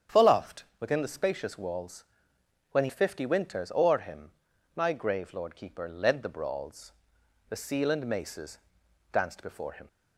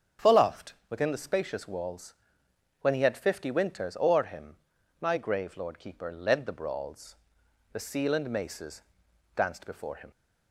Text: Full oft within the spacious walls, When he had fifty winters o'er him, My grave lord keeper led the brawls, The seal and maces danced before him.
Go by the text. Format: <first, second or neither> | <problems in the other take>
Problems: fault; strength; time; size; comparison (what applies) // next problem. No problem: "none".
second | starts louder than the rest; strong; until 1.2 s; 8.5 dB; strong in the second // pauses between "oft" and "within"; slight; at 0.6 s; 0.16 s long; slight in the second // skips "had"; at 2.9 s // pauses between "maces" and "danced"; noticeable; at 8.5 s; 0.54 s long; noticeable in the second